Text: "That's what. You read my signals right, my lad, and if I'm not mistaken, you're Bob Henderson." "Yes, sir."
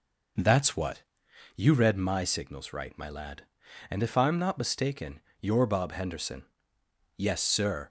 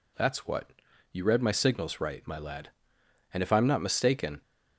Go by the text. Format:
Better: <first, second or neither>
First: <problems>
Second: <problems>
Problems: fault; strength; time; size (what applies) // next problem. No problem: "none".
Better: first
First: none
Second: stops before "you're Bob Henderson Yes sir"; at 4.4 s